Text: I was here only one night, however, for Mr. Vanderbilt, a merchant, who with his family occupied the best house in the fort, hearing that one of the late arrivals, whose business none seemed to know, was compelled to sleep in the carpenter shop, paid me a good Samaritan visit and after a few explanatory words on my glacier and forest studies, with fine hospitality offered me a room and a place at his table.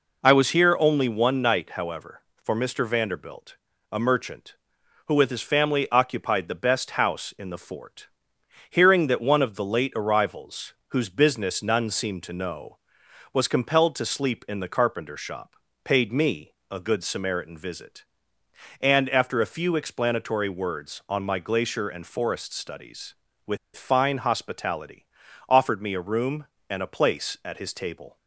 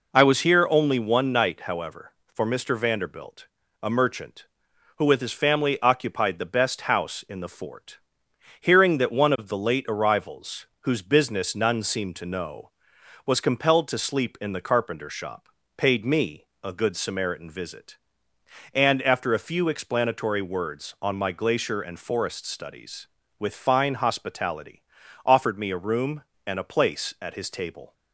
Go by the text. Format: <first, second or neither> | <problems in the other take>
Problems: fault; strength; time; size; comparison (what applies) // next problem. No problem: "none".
second | pauses between "me" and "a"; slight; at 16.5 s; 0.18 s long; slight in the second // pauses between "with" and "fine"; slight; at 23.5 s; 0.18 s long // pauses between "hospitality" and "offered"; at 25.0 s; 0.42 s long; also in the second